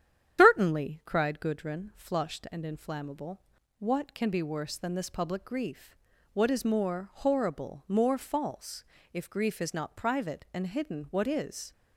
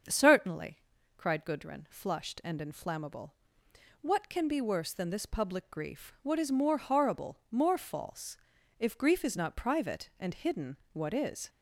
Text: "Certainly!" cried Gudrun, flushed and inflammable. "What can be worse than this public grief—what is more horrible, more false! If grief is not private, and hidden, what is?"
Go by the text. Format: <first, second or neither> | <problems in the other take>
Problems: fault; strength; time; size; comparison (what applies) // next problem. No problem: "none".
second | loses the start of "Certainly"; at 0.3 s; 145 ms // starts louder than the rest; strong; until 1.4 s; 10 dB; also in the second